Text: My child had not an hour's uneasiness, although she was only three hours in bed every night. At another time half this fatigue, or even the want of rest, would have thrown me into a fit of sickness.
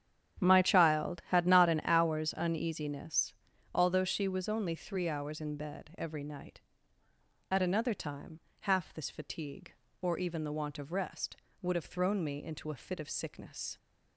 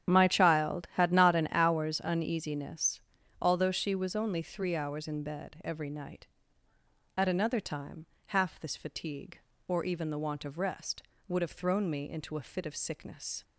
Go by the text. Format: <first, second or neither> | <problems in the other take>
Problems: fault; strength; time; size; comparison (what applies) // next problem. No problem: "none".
first | loses the start of "My"; at 0.0 s; 50 ms // starts louder than the rest; strong; until 1.1 s; 9.5 dB; strong in the first // pauses between "time" and "half"; slight; at 8.0 s; 0.22 s long; slight in the first